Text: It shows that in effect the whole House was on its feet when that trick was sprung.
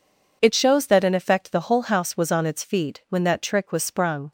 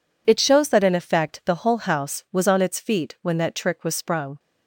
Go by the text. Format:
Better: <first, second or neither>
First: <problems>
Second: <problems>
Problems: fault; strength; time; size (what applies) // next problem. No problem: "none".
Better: neither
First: none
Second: none